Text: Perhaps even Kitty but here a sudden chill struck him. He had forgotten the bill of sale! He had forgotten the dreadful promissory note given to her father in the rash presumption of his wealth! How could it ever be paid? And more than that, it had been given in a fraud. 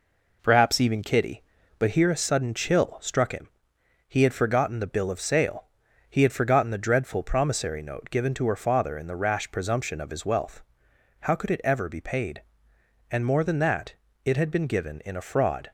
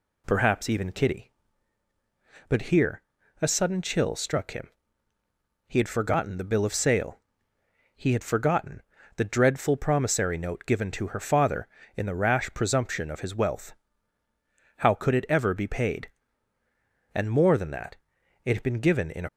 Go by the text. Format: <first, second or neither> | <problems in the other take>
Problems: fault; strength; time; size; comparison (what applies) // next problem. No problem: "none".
first | pauses between "here" and "a"; at 3.0 s; 0.40 s long // pauses between "forgotten" and "the"; slight; at 8.8 s; 0.34 s long // stops before "fraud"; at 19.2 s